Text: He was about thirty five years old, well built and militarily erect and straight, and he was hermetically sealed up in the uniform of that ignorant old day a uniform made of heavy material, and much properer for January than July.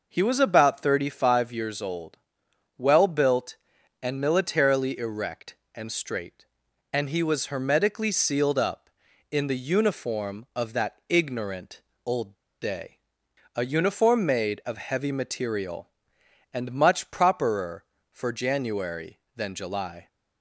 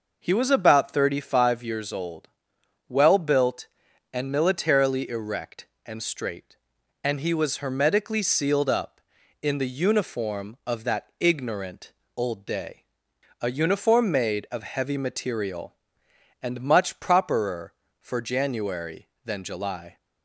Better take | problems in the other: second | pauses between "ignorant" and "old"; slight; at 11.8 s; 0.24 s long; slight in the second // pauses between "old" and "day"; slight; at 12.3 s; 0.26 s long // pauses between "day" and "a"; noticeable; at 12.9 s; 0.58 s long; noticeable in the second

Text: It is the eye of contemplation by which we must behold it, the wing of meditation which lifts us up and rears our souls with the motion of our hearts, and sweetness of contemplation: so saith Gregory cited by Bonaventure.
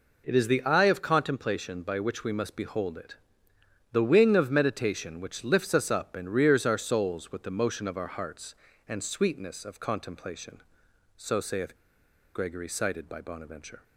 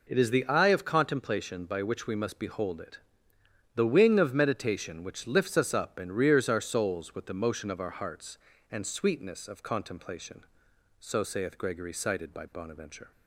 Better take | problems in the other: second | pauses between "saith" and "Gregory"; noticeable; at 11.7 s; 0.60 s long

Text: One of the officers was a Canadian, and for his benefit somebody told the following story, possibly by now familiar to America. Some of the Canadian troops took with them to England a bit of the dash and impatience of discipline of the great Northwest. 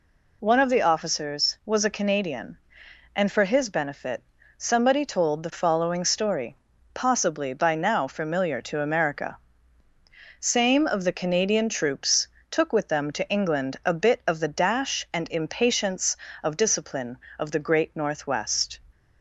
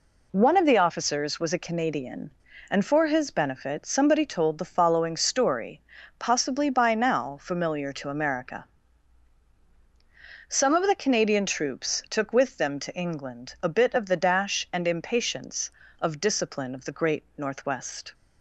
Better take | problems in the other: second | pauses between "benefit" and "somebody"; slight; at 4.2 s; 0.32 s long // says "Same" for "Some"; at 10.3 s // pauses between "troops" and "took"; slight; at 12.2 s; 0.22 s long

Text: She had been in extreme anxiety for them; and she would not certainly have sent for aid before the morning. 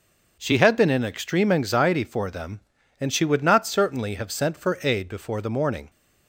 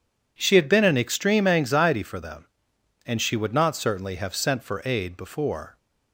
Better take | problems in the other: first | stops before "the morning"; at 5.7 s

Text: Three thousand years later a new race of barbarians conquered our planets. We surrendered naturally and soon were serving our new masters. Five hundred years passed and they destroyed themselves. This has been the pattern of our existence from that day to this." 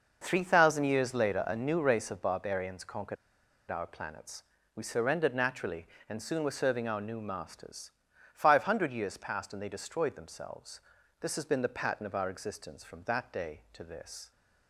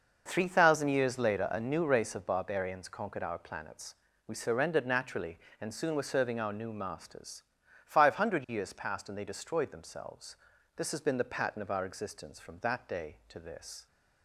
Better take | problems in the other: second | pauses between "conquered" and "our"; noticeable; at 3.1 s; 0.55 s long

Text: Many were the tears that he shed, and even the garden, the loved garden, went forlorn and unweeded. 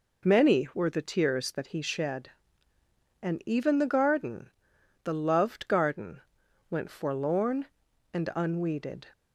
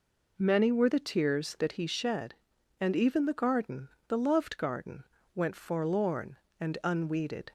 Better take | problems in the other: neither | none

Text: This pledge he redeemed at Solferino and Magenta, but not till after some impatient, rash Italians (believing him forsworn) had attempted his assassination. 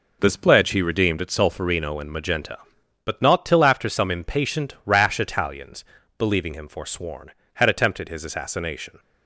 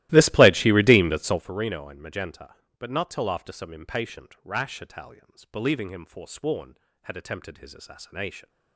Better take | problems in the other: first | starts louder than the rest; strong; until 1.5 s; 17 dB

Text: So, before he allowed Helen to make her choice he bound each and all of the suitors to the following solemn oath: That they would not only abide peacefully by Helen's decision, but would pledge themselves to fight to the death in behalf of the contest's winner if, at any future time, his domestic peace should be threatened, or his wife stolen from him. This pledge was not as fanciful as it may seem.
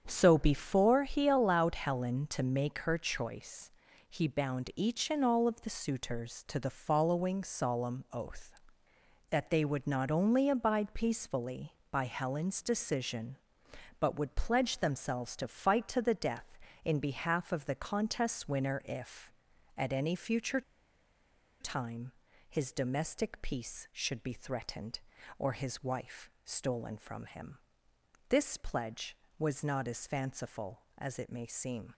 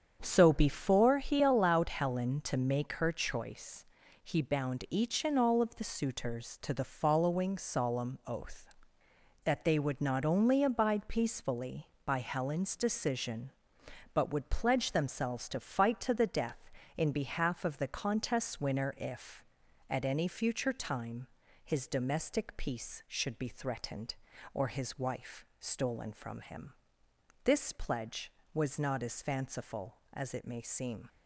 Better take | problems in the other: second | starts louder than the rest; strong; until 1.0 s; 7.5 dB; strong in the second // pauses between "choice" and "he"; at 3.6 s; 0.38 s long; also in the second // pauses between "future" and "time"; at 20.6 s; 0.98 s long

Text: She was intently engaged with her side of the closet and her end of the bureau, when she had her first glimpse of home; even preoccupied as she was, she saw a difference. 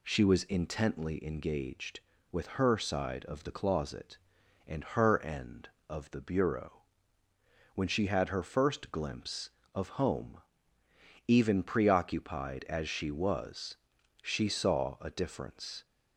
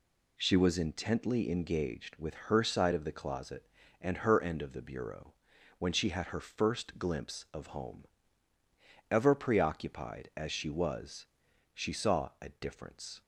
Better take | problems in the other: first | says "ever" for "even"; at 9.0 s

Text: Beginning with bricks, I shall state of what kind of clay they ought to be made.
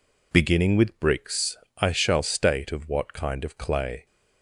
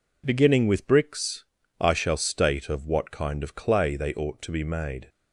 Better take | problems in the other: second | stops before "they ought to be made"; at 4.0 s

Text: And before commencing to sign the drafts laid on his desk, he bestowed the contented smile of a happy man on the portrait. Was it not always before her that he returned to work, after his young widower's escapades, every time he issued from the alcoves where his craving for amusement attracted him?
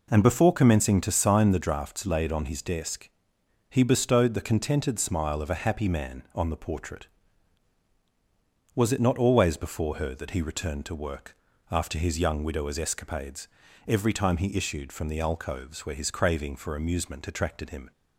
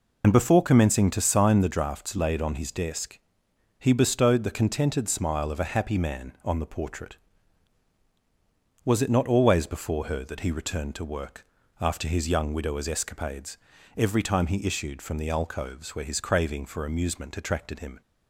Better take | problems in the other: first | loses the start of "And"; at 0.2 s; 70 ms

